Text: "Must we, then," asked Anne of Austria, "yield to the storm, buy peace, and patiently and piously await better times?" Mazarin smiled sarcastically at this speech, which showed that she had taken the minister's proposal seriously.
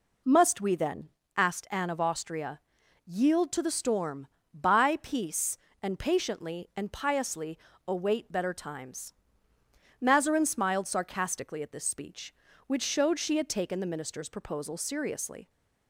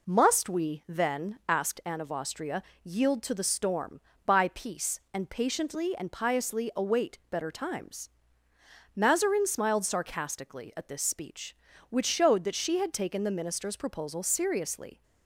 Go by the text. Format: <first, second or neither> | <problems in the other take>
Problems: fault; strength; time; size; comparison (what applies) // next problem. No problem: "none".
second | pauses between "piously" and "await"; slight; at 7.5 s; 0.28 s long // skips "that"; at 13.1 s